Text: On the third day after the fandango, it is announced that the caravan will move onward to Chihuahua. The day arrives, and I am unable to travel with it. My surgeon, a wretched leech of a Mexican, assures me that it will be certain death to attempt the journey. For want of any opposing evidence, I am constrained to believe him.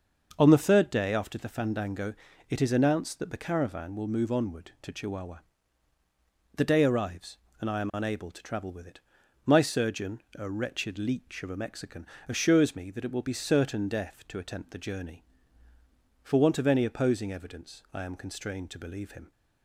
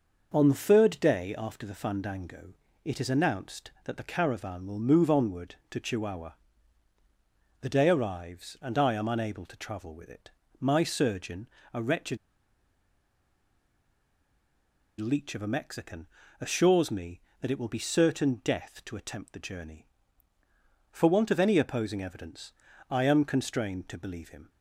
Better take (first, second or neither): first